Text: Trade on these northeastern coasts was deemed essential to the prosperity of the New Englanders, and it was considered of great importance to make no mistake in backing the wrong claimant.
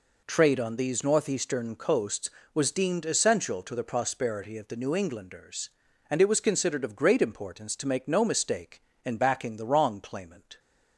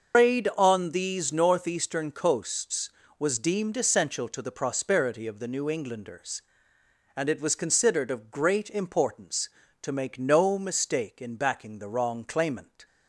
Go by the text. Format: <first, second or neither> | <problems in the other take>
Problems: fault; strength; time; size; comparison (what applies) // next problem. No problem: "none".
first | loses the start of "Trade"; at 0.1 s; 160 ms // starts louder than the rest; until 1.2 s; 6.5 dB